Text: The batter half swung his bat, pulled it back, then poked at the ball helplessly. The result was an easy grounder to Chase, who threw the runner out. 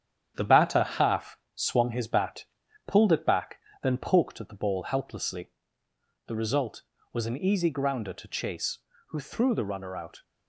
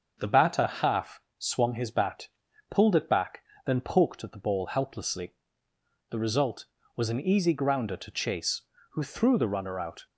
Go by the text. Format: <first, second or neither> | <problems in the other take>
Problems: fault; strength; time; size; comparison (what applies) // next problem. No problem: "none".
second | gets quieter; noticeable; throughout; 4.5 dB // starts louder than the rest; strong; until 1.3 s; 9.5 dB; also in the second // pauses between "half" and "swung"; slight; at 1.3 s; 0.18 s long; slight in the second